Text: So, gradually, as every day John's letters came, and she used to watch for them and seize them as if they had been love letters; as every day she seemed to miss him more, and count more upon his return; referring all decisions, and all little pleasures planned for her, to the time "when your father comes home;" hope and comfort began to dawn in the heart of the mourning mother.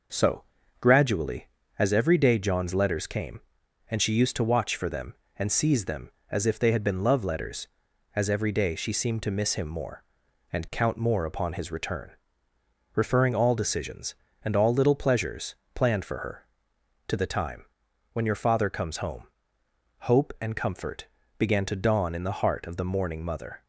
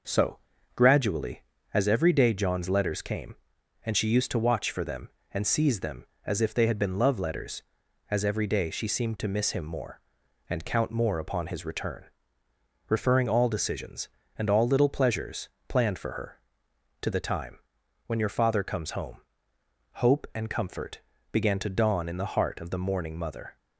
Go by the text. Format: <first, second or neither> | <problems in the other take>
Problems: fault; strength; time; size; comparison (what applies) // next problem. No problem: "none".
neither | pauses between "pleasures" and "planned"; slight; the same in both // pauses between "time" and "when"; noticeable; the same in both // pauses between "comfort" and "began"; slight; the same in both